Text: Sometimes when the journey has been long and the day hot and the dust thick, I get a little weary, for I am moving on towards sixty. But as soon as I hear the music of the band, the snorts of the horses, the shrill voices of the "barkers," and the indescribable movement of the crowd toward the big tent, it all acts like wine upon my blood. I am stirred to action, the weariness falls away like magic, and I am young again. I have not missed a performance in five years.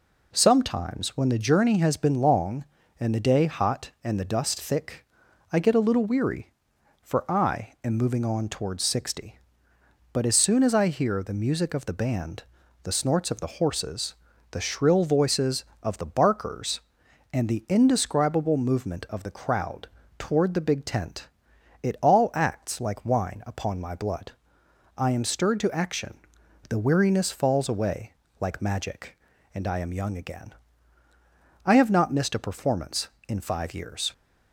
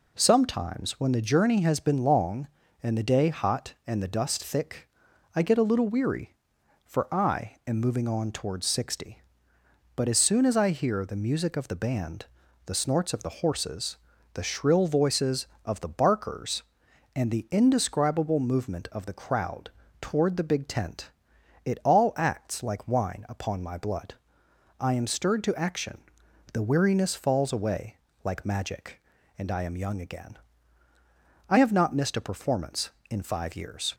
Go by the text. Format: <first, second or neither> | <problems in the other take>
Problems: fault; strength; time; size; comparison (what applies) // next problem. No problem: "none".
neither | pauses between "crowd" and "toward"; slight; the same in both // pauses between "away" and "like"; slight; the same in both